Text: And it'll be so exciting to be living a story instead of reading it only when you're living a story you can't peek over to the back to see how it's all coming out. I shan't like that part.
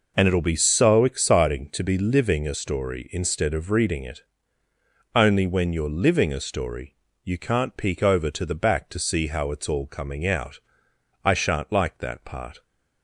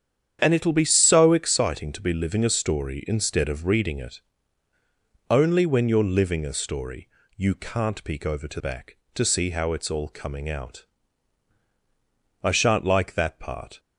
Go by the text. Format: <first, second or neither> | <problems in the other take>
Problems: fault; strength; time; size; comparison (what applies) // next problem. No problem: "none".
first | starts louder than the rest; strong; until 1.4 s; 8.5 dB // pauses between "it" and "only"; at 4.1 s; 1.1 s long; noticeable in the first // pauses between "story" and "you"; slight; at 7.0 s; 0.28 s long; slight in the first // skips "the"; at 8.5 s